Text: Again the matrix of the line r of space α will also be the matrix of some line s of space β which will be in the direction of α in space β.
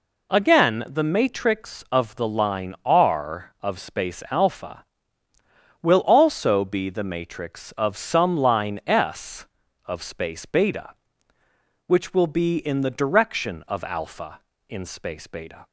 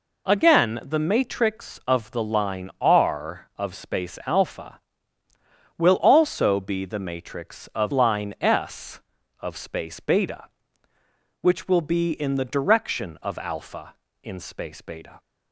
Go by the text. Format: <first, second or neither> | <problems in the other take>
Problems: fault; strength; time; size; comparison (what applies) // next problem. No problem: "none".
first | skips "some"; at 7.9 s